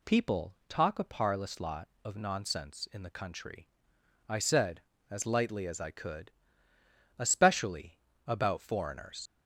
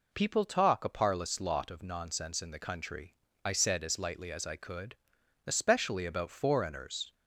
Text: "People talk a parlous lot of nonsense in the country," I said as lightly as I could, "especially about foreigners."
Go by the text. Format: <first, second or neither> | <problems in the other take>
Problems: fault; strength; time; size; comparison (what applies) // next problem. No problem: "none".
second | pauses between "especially" and "about"; slight; at 7.9 s; 0.26 s long // leaves "foreigners" unfinished; at 9.2 s; 85 ms